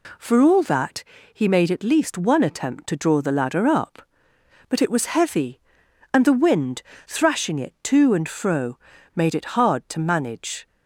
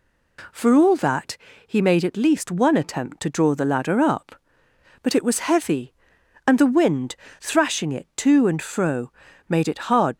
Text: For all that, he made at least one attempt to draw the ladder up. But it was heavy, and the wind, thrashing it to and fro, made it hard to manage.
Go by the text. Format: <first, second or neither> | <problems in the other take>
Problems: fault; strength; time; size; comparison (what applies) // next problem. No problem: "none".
first | stops before "to manage"; at 10.1 s